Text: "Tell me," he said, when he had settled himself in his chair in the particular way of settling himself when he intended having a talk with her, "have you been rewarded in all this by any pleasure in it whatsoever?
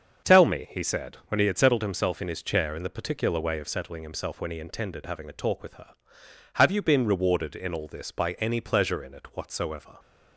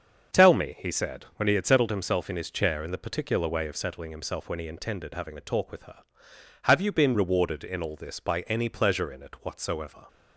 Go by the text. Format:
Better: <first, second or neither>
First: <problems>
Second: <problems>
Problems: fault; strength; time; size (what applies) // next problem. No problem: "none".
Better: neither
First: starts louder than the rest; until 1.3 s; 6.5 dB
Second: starts louder than the rest; until 1.4 s; 6.5 dB